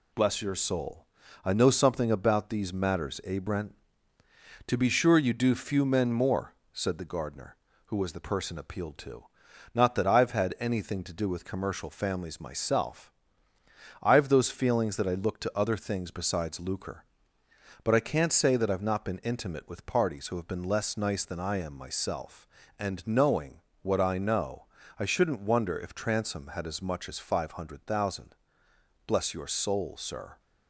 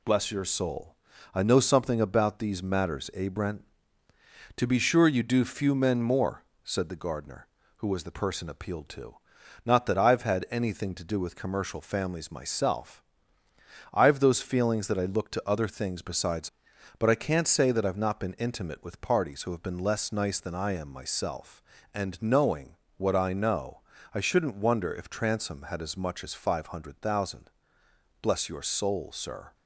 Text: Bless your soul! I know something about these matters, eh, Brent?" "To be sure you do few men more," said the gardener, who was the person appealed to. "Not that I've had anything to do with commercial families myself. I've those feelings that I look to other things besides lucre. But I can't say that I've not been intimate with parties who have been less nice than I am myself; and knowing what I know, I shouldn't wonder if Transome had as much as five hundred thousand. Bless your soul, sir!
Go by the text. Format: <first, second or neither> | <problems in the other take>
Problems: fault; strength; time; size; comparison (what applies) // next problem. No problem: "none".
first | skips "lucre"; at 16.7 s // pauses between "knowing" and "what"; slight; at 22.7 s; 0.22 s long; slight in the first